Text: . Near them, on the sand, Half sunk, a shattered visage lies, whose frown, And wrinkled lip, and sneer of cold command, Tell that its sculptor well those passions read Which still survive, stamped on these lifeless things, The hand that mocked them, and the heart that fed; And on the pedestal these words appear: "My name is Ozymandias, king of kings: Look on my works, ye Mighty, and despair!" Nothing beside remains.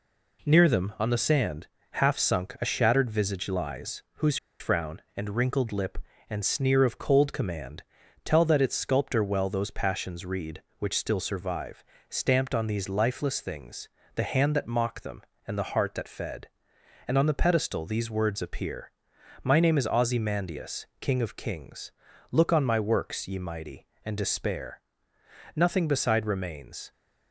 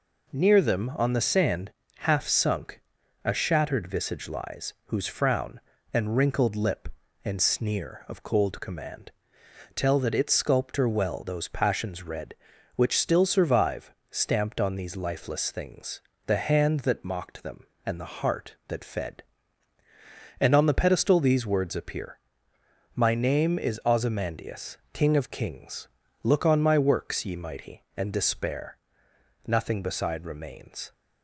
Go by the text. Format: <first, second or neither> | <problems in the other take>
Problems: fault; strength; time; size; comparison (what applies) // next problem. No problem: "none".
second | pauses between "whose" and "frown"; slight; at 4.3 s; 0.21 s long